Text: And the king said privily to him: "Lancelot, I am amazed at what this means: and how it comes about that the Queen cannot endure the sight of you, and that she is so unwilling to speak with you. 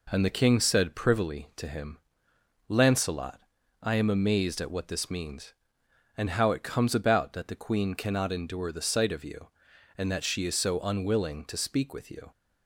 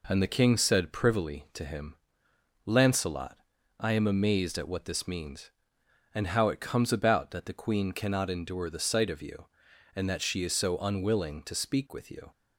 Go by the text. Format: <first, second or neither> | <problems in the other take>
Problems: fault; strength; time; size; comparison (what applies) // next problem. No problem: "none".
neither | none